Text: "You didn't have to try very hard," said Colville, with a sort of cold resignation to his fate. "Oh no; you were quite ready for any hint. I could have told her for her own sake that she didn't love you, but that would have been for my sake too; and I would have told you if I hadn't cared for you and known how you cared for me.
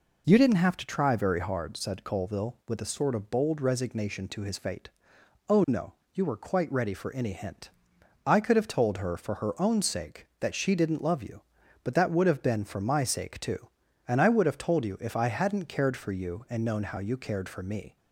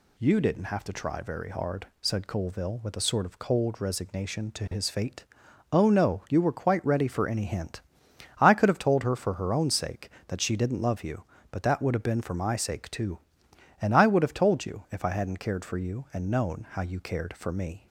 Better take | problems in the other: second | says "bold" for "cold"; at 3.2 s

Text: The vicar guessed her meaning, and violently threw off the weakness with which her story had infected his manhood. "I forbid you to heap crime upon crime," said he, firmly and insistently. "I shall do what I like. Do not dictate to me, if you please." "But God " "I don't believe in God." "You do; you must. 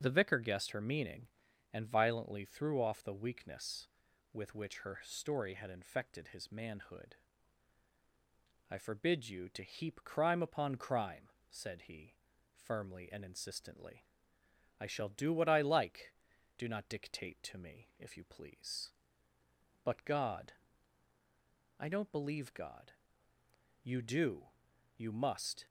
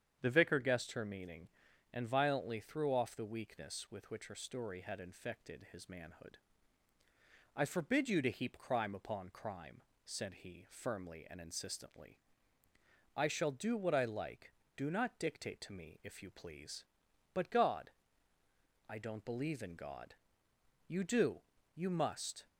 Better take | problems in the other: second | starts louder than the rest; until 1.0 s; 7 dB; strong in the second // skips "in"; at 22.5 s

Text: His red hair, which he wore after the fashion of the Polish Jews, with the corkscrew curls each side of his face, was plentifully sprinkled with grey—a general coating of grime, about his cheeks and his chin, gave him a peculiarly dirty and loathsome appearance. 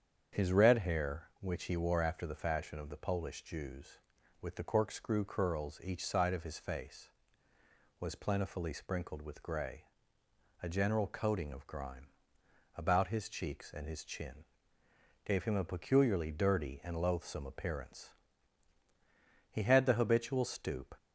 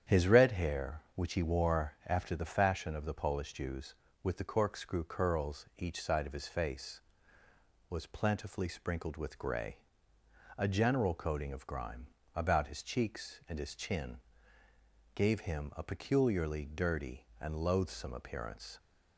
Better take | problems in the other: second | starts louder than the rest; strong; until 1.4 s; 7.5 dB; strong in the second // goes on to say "He had the habitual stoop"; from 19.5 s on; 1.4 s long

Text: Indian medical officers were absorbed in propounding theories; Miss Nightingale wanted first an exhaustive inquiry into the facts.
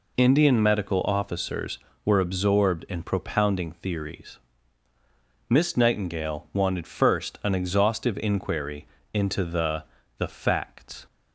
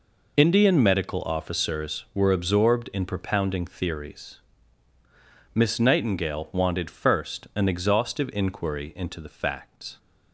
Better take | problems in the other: second | pauses between "inquiry" and "into"; slight; at 8.8 s; 0.26 s long // says "the" twice; at 10.1 s

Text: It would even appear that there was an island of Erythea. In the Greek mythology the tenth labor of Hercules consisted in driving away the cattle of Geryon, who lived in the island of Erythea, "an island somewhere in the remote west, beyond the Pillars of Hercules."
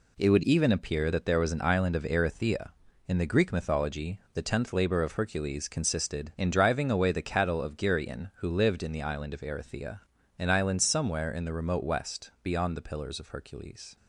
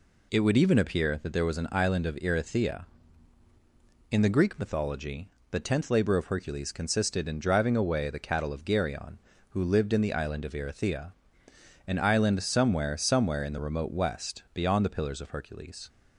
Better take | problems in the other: first | pauses between "mythology" and "the"; slight; at 5.2 s; 0.22 s long; slight in the first // says "somewhere" twice; at 12.9 s

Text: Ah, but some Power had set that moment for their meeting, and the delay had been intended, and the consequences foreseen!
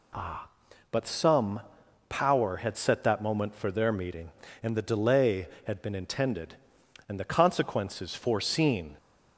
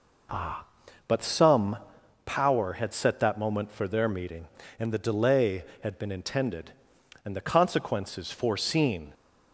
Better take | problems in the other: first | starts louder than the rest; noticeable; until 2.2 s; 4.5 dB // pauses between "some" and "Power"; noticeable; at 1.7 s; 0.50 s long; noticeable in the first

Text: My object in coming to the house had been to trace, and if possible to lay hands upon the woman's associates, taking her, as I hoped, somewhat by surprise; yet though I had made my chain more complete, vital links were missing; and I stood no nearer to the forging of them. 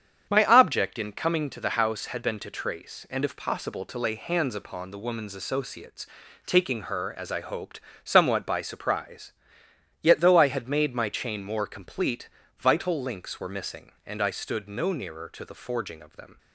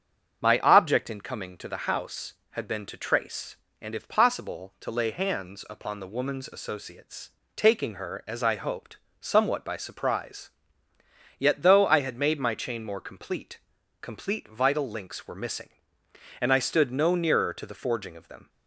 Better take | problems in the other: first | starts louder than the rest; strong; until 1.4 s; 7 dB; strong in the first // says "complete" twice; at 14.0 s

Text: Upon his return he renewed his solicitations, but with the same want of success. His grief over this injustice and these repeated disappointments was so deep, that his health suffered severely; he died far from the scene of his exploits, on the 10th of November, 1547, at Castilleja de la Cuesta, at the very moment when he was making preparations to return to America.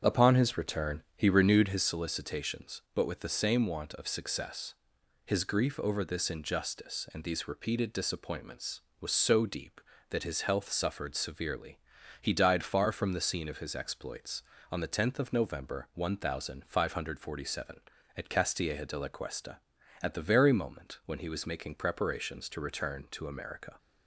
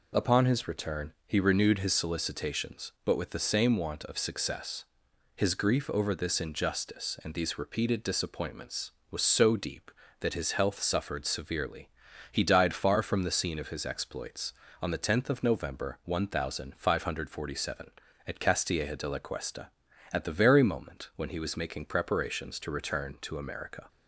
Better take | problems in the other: second | starts louder than the rest; strong; until 1.8 s; 8 dB

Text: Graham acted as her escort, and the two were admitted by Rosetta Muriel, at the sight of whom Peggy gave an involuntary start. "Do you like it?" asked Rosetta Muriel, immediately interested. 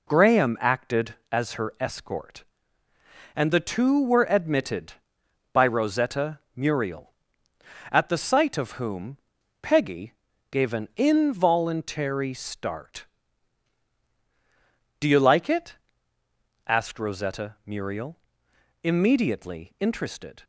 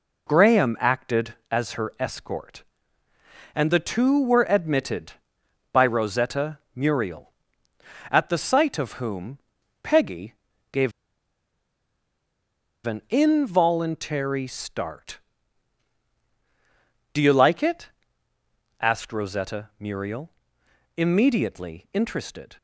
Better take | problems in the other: first | pauses between "Rosetta" and "Muriel"; slight; at 6.5 s; 0.18 s long; slight in the first // pauses between "whom" and "Peggy"; at 9.3 s; 0.44 s long; also in the first // pauses between "Peggy" and "gave"; at 10.3 s; 0.38 s long; also in the first // pauses between "gave" and "an"; strong; at 10.9 s; 1.9 s long

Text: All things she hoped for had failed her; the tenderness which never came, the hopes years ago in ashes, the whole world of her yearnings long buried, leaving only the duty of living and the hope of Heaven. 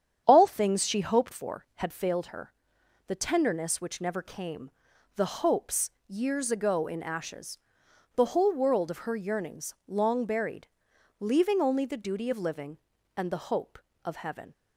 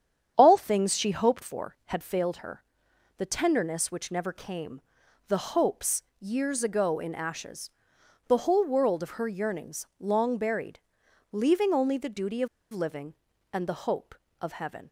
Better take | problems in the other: first | starts louder than the rest; strong; until 1.3 s; 8.5 dB; strong in the first // pauses between "hopes" and "years"; slight; at 6.0 s; 0.16 s long; slight in the first // pauses between "of" and "living"; slight; at 12.4 s; 0.25 s long

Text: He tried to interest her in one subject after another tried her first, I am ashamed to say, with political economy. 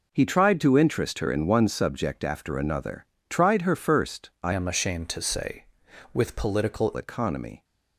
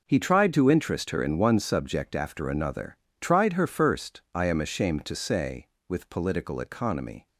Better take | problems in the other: second | pauses between "another" and "tried"; slight; at 3.0 s; 0.24 s long; slight in the second // changes voice from "am" to "political"; from 4.5 to 6.9 s; 2.4 s long

